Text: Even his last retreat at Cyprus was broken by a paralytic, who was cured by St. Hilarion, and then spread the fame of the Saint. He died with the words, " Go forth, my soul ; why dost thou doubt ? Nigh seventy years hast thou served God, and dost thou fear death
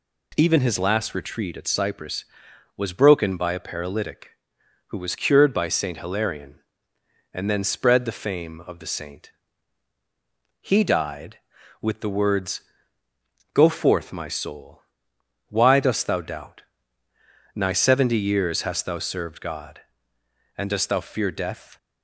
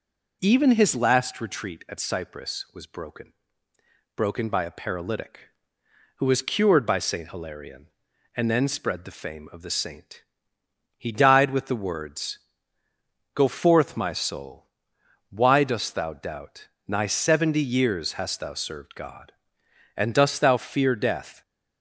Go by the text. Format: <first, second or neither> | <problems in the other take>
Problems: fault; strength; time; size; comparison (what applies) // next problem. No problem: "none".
first | says "broken" twice; at 4.1 s